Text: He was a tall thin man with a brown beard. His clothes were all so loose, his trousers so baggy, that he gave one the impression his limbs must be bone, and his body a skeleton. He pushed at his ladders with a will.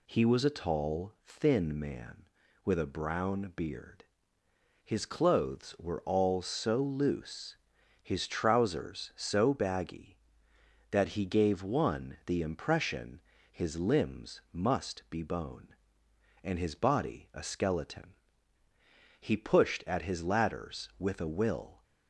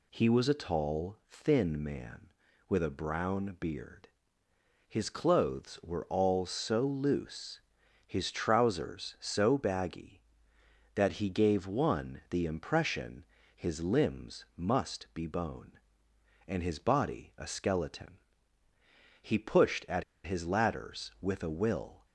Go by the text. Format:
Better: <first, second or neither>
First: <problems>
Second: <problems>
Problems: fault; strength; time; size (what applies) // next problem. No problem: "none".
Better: first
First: pauses between "impression" and "his"; slight; at 13.2 s; 0.30 s long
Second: pauses between "impression" and "his"; slight; at 13.2 s; 0.30 s long // pauses between "at" and "his"; slight; at 20.0 s; 0.21 s long